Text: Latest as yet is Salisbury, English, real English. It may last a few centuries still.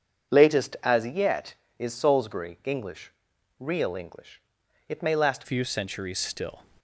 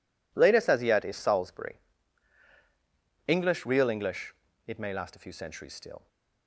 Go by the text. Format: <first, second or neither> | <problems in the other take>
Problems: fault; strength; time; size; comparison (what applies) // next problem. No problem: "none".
second | changes voice at "few"; from 5.4 s on; 1.2 s long